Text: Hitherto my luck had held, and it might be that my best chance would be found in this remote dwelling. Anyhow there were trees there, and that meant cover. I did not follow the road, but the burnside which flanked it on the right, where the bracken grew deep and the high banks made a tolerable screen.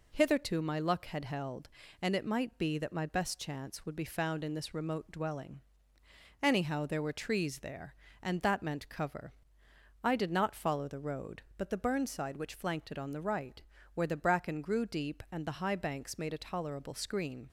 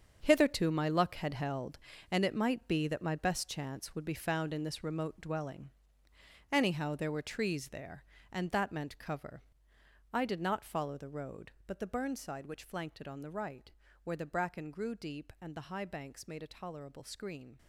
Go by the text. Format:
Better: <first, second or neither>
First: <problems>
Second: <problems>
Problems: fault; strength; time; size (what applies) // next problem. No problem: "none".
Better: first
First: none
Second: gets quieter; strong; throughout; 11.5 dB